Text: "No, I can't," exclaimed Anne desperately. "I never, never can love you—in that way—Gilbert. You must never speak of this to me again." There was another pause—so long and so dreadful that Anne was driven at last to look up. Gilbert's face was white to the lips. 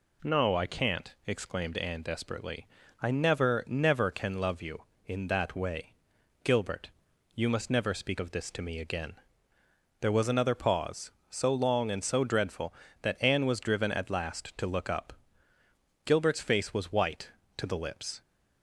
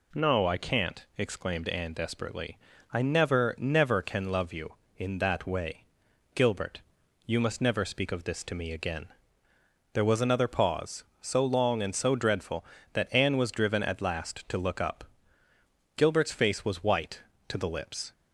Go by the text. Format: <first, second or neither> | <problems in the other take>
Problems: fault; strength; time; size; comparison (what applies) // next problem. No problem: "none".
neither | none